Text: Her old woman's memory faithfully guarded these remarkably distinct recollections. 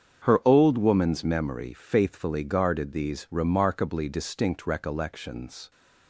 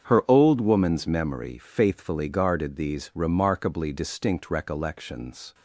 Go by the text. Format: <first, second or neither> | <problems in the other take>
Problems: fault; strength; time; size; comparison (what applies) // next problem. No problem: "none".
neither | starts louder than the rest; strong; the same in both